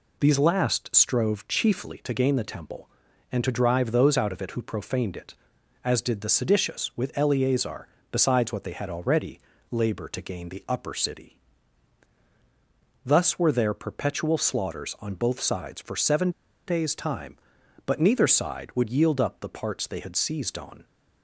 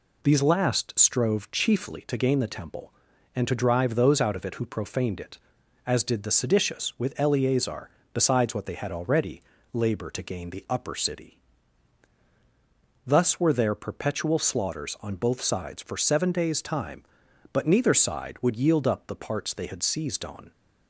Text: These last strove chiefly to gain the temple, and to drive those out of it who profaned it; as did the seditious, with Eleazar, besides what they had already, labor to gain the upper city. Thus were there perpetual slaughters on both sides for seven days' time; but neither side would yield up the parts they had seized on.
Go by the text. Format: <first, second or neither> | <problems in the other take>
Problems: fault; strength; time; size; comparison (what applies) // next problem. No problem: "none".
second | pauses between "seven" and "days"; slight; at 16.3 s; 0.35 s long